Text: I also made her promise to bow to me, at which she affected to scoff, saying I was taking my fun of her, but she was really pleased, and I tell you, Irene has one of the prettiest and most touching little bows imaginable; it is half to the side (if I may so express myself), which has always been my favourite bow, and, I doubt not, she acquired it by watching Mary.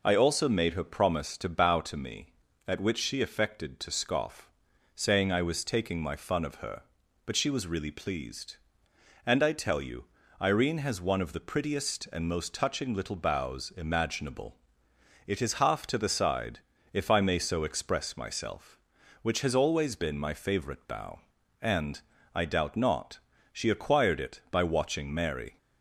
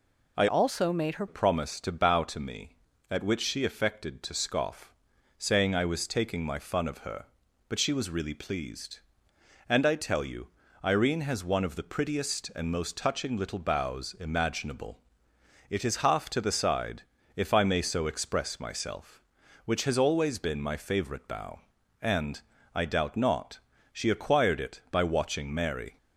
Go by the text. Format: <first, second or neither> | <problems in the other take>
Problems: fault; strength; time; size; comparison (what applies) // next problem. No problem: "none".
first | changes voice from "also" to "her"; from 0.4 to 1.2 s; 0.8 s long